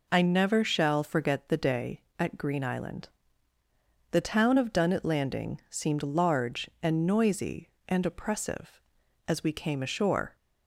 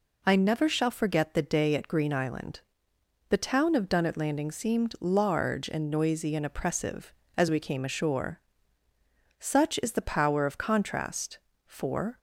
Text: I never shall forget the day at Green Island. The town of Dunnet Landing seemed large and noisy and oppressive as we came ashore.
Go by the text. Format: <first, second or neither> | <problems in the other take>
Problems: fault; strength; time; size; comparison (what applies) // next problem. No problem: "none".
first | goes on to say "Such is the power of contrast for"; strong; from 9.3 s on; 2.8 s long